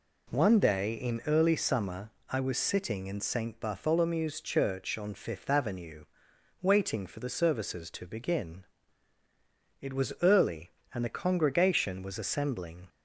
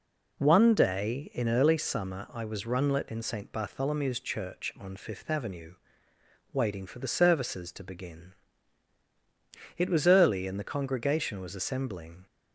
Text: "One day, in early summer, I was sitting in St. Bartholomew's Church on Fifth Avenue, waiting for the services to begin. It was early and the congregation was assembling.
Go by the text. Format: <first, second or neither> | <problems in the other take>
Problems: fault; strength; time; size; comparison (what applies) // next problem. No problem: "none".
first | says "runlet" for "sitting"; at 2.6 s